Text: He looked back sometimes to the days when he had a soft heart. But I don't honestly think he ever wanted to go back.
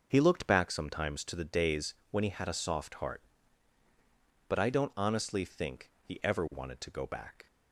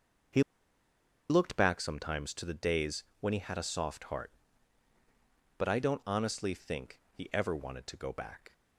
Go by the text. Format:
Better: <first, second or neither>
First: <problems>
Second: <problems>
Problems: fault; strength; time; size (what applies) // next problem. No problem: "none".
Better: first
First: pauses between "days" and "when"; slight; at 1.9 s; 0.16 s long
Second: pauses between "He" and "looked"; noticeable; at 0.4 s; 0.88 s long // pauses between "days" and "when"; slight; at 3.0 s; 0.16 s long